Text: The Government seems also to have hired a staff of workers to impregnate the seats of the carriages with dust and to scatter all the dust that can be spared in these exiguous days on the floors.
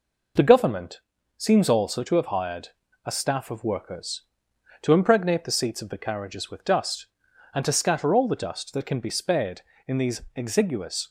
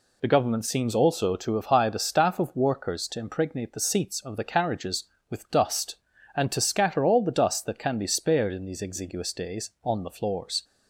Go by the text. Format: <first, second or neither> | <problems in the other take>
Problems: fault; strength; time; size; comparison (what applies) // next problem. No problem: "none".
second | pauses between "Government" and "seems"; at 1.0 s; 0.38 s long // pauses between "hired" and "a"; at 2.6 s; 0.38 s long // stops before "days on the floors"; at 11.0 s